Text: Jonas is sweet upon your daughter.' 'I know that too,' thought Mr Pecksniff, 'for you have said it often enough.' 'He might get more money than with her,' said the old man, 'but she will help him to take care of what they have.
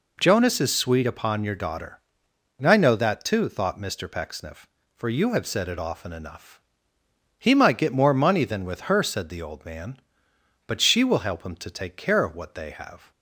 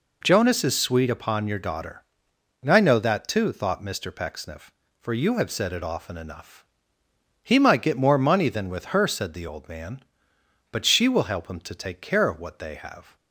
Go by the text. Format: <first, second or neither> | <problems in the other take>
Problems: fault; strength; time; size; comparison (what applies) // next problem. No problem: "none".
neither | none